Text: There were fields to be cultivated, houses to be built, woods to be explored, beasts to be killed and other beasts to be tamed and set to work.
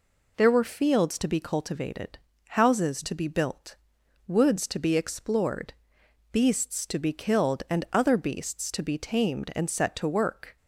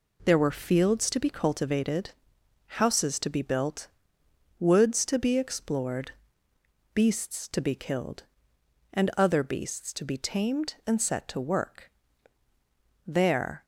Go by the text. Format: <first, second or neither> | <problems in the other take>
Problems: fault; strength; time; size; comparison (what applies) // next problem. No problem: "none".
first | goes on to say "There"; from 13.0 s on; 0.58 s long